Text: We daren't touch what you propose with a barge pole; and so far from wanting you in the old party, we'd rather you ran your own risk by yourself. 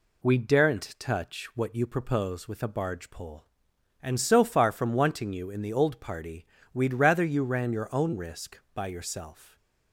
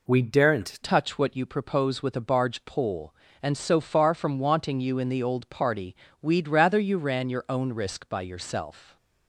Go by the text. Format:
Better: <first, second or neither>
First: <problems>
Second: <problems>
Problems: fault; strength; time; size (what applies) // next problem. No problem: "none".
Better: first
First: none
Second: changes voice at "touch"; from 0.8 s on; 8.1 s long